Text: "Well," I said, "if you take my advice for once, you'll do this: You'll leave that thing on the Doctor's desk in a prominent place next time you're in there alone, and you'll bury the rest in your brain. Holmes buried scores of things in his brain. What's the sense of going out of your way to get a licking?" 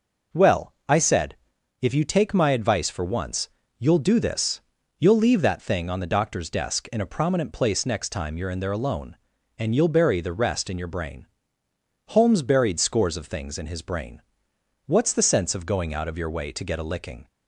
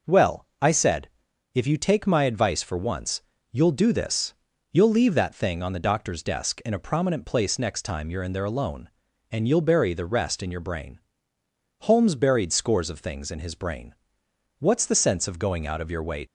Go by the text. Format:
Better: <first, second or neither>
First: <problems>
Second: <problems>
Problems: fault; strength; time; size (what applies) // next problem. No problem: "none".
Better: first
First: none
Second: stops before "to get a licking"; at 16.2 s